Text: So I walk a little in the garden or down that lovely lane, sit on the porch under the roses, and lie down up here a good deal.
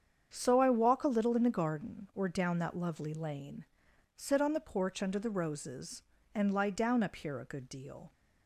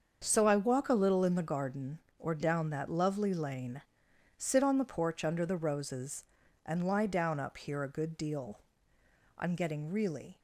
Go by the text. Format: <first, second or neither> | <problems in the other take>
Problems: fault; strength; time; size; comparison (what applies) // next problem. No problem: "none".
first | starts louder than the rest; until 1.2 s; 6.5 dB; strong in the first // goes on to say "I'm getting really"; noticeable; from 9.3 s on; 1.0 s long